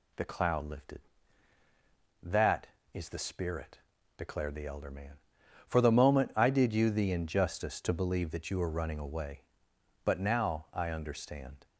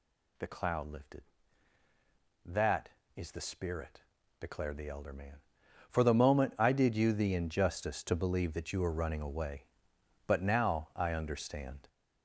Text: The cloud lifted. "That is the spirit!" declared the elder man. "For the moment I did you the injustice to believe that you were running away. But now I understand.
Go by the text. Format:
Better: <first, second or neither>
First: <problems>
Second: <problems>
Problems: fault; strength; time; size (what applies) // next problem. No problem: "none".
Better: first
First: none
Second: gets louder; throughout; 7 dB